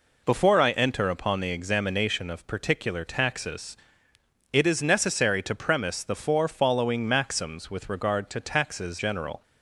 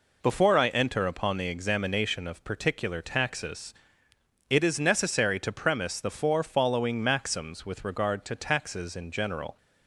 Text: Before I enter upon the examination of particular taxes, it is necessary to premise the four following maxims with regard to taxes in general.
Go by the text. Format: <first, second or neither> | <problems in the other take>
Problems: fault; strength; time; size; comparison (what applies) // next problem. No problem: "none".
second | skips "in"; at 8.9 s